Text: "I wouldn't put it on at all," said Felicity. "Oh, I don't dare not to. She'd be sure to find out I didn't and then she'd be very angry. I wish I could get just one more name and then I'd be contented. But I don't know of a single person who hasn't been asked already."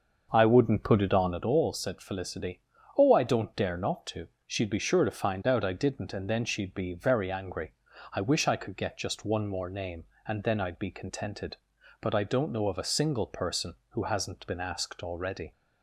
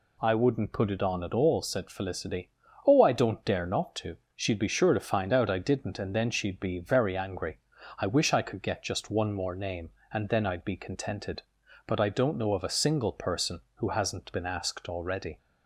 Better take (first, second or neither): second